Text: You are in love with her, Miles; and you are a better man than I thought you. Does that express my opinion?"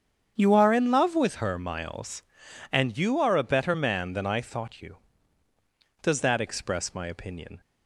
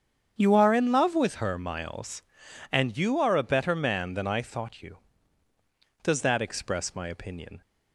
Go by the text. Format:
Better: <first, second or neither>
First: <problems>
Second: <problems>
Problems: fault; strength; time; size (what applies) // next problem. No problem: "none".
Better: neither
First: starts louder than the rest; strong; until 1.3 s; 8 dB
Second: starts louder than the rest; strong; until 1.4 s; 8 dB